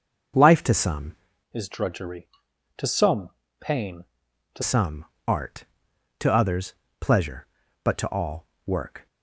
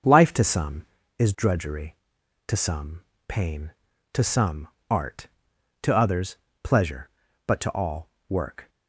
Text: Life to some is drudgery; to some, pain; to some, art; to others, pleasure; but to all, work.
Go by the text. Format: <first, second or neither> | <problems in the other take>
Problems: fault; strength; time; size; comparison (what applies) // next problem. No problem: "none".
second | changes voice from "is" to "to"; from 1.5 to 4.6 s; 3.1 s long